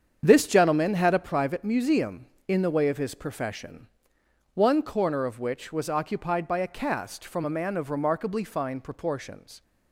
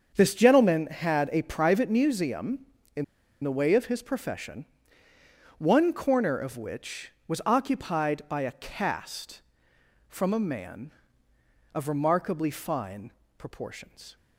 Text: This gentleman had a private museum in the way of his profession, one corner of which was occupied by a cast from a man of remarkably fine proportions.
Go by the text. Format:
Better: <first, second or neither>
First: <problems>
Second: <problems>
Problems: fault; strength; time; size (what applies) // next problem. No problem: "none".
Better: first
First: starts louder than the rest; strong; until 1.2 s; 7.5 dB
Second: starts louder than the rest; until 1.1 s; 7 dB // pauses between "in" and "the"; at 3.0 s; 0.38 s long // pauses between "fine" and "proportions"; slight; at 13.1 s; 0.26 s long